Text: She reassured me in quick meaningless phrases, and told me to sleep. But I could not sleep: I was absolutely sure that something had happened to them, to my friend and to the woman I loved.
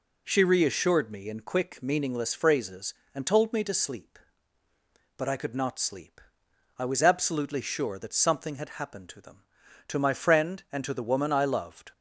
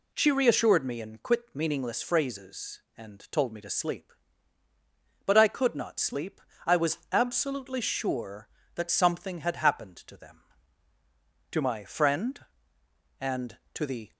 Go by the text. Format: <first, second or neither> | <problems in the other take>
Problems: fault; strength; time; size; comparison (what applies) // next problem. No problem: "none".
first | stops before "woman I loved"; at 14.1 s